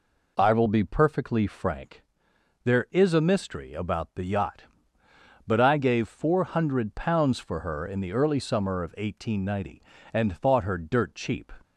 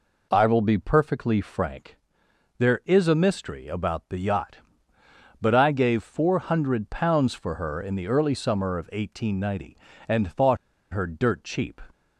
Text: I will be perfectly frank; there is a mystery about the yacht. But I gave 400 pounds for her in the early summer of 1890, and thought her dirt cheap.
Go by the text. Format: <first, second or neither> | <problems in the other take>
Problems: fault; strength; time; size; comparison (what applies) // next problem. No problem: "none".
first | pauses between "thought" and "her"; at 10.5 s; 0.36 s long